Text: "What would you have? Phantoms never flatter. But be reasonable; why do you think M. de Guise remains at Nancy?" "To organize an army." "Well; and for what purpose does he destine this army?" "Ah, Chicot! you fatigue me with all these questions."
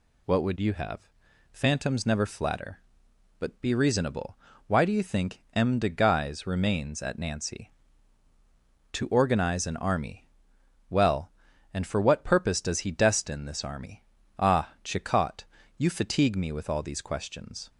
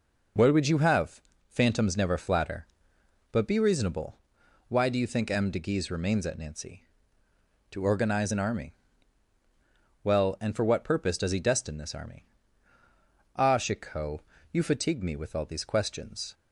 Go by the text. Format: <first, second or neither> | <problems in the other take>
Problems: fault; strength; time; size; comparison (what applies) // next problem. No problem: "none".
neither | none